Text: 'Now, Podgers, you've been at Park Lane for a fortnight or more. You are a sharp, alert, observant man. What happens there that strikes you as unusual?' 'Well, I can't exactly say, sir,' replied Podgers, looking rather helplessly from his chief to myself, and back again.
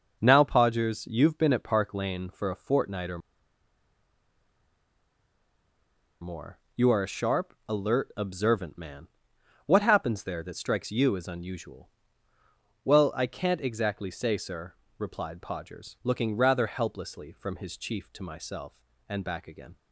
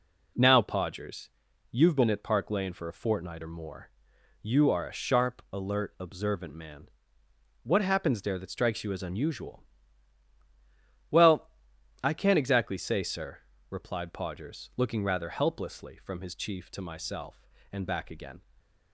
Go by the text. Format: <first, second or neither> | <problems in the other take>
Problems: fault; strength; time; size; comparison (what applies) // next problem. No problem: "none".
second | pauses between "or" and "more"; strong; at 3.1 s; 3.0 s long